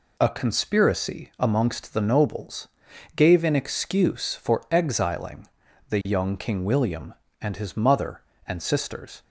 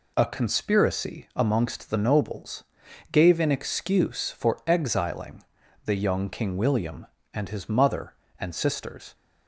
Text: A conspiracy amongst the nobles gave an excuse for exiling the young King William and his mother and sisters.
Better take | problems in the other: neither | pauses between "nobles" and "gave"; noticeable; the same in both // pauses between "exiling" and "the"; the same in both

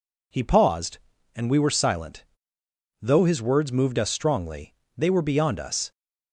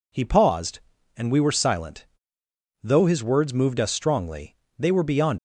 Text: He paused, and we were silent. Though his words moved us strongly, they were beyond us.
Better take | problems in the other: first | stops before "us"; at 5.3 s

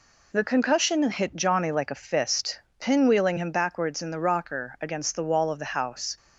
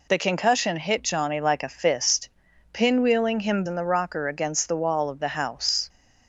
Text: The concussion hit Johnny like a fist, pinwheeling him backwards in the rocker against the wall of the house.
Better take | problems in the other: first | skips "backwards"; at 3.6 s

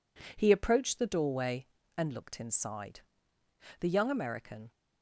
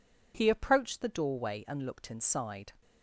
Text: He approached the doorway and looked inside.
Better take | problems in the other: second | goes on to say "The young American"; noticeable; from 3.8 s on; 0.90 s long

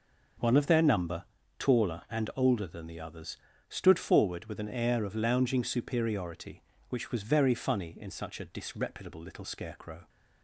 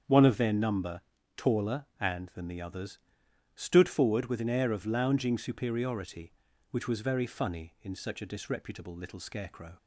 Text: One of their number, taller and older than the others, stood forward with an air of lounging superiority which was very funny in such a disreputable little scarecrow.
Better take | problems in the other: first | starts louder than the rest; strong; until 1.4 s; 7.5 dB; noticeable in the first // skips "older"; at 2.2 s

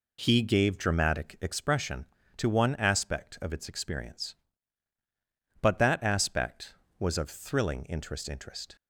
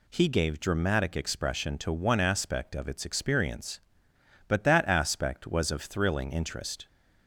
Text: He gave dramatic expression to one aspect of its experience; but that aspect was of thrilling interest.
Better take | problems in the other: second | says "interest" twice; at 8.2 s

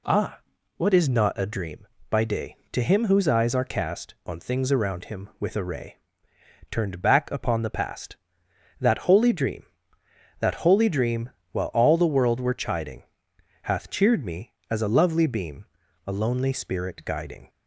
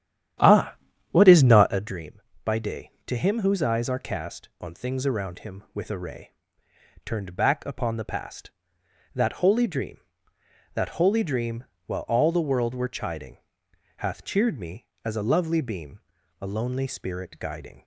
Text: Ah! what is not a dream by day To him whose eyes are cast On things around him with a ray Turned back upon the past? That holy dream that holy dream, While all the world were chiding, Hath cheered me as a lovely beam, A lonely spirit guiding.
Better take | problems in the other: first | starts louder than the rest; strong; until 1.8 s; 10.5 dB // pauses between "ray" and "Turned"; noticeable; at 6.2 s; 0.74 s long; noticeable in the first

